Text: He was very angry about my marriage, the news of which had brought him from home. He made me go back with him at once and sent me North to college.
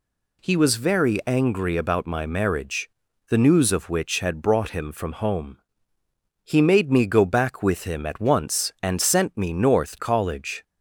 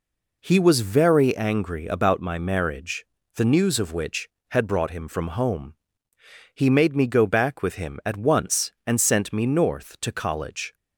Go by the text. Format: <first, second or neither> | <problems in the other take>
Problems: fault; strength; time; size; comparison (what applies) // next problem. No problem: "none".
second | skips "to"; at 9.9 s